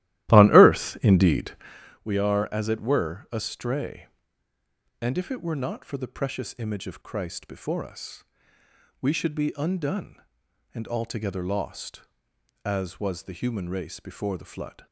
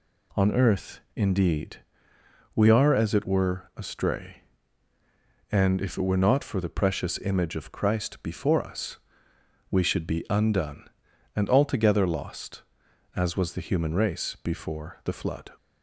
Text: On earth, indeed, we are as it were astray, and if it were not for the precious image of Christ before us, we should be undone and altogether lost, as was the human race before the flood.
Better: second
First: starts louder than the rest; strong; until 2.0 s; 15 dB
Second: none

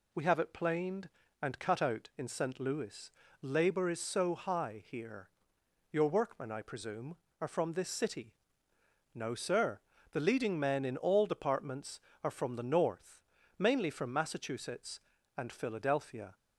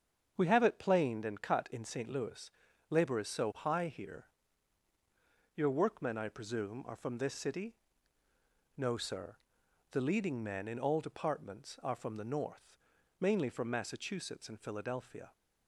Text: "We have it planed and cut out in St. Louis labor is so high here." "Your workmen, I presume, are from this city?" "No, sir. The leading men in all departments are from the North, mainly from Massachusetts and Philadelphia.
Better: first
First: pauses between "Louis" and "labor"; slight; at 3.0 s; 0.32 s long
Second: starts louder than the rest; strong; until 1.3 s; 7.5 dB // skips "out"; at 1.6 s // pauses between "Louis" and "labor"; at 2.5 s; 0.40 s long

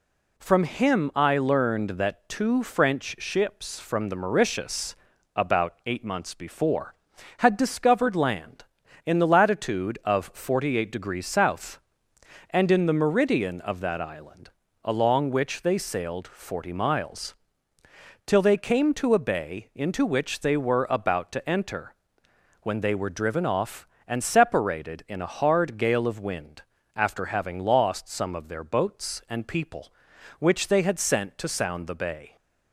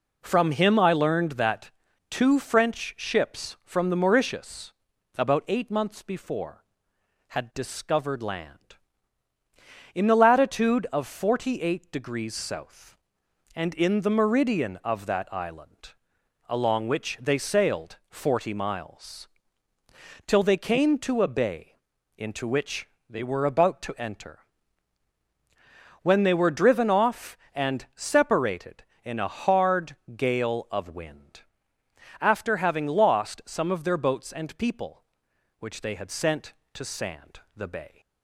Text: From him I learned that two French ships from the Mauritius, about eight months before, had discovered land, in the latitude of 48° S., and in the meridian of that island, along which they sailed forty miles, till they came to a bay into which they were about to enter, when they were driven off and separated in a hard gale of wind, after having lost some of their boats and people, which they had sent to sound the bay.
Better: first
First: none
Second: pauses between "that" and "two"; slight; at 1.7 s; 0.36 s long // pauses between "bay" and "into"; at 21.7 s; 0.42 s long // pauses between "which" and "they"; slight; at 22.8 s; 0.20 s long // pauses between "hard" and "gale"; slight; at 29.9 s; 0.20 s long // says "sand" for "sound"; at 36.8 s

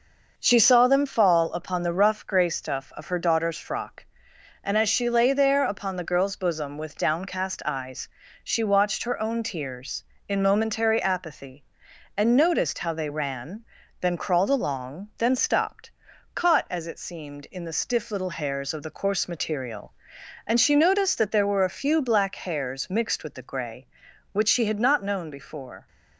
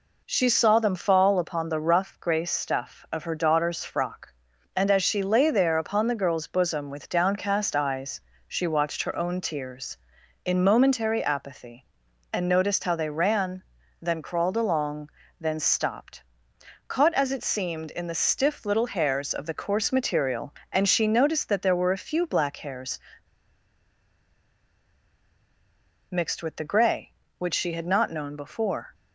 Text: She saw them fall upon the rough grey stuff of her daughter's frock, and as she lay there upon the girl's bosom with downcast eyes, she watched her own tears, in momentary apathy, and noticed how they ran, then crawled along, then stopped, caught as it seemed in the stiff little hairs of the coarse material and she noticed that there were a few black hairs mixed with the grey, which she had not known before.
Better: first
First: none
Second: pauses between "hairs" and "mixed"; strong; at 22.9 s; 3.1 s long

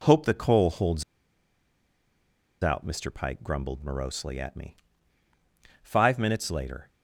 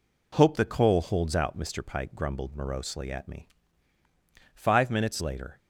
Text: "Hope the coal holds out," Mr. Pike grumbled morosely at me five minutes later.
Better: second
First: pauses between "holds" and "out"; strong; at 1.0 s; 1.6 s long // pauses between "me" and "five"; at 4.7 s; 1.0 s long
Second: pauses between "me" and "five"; at 3.4 s; 1.0 s long

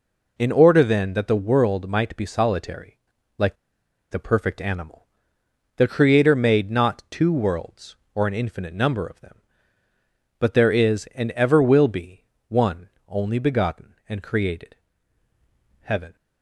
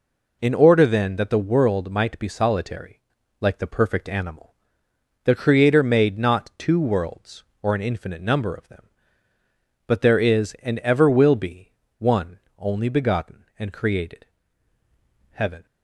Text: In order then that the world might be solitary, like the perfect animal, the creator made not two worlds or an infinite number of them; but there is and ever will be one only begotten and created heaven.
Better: second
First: pauses between "like" and "the"; noticeable; at 3.5 s; 0.56 s long // pauses between "be" and "one"; slight; at 12.2 s; 0.22 s long // pauses between "one" and "only"; slight; at 12.8 s; 0.18 s long // pauses between "created" and "heaven"; at 14.7 s; 1.0 s long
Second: pauses between "be" and "one"; slight; at 11.7 s; 0.25 s long // pauses between "one" and "only"; slight; at 12.3 s; 0.18 s long // pauses between "created" and "heaven"; at 14.2 s; 1.0 s long

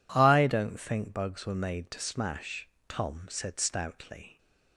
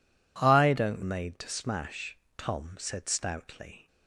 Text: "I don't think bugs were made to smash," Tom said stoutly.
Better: first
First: none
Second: skips "think bugs were"; at 1.0 s

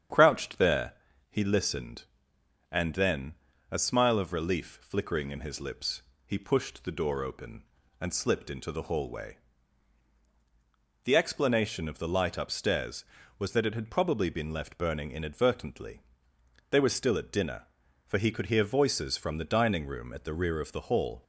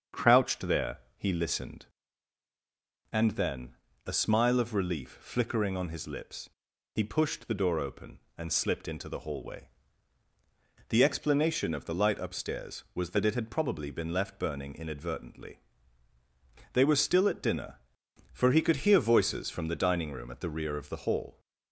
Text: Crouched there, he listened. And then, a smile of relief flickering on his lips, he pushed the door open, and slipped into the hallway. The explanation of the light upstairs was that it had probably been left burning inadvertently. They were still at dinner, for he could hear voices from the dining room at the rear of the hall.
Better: second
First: starts louder than the rest; strong; until 1.5 s; 8.5 dB // says "in" for "on"; at 5.3 s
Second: starts louder than the rest; until 1.3 s; 7 dB

